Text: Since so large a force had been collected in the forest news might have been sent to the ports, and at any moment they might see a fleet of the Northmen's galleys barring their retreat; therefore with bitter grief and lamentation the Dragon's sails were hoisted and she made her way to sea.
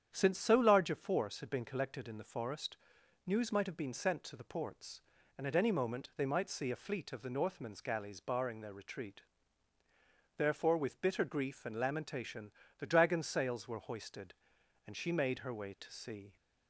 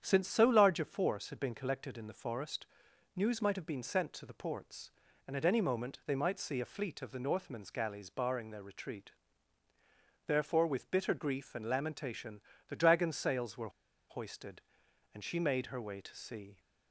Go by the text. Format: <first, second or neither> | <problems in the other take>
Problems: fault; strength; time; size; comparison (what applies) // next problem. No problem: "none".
first | starts louder than the rest; strong; until 1.0 s; 9 dB; strong in the first // pauses between "forest" and "news"; noticeable; at 2.6 s; 0.50 s long; noticeable in the first // pauses between "lamentation" and "the"; slight; at 12.4 s; 0.26 s long; slight in the first // pauses between "were" and "hoisted"; at 13.6 s; 0.40 s long